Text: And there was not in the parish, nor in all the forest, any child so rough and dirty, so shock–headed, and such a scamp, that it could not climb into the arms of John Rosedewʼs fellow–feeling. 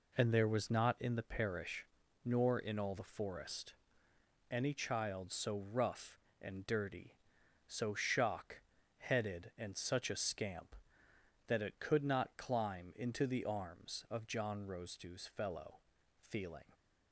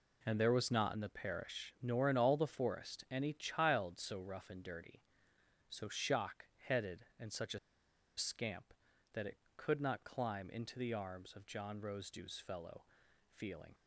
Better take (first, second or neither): first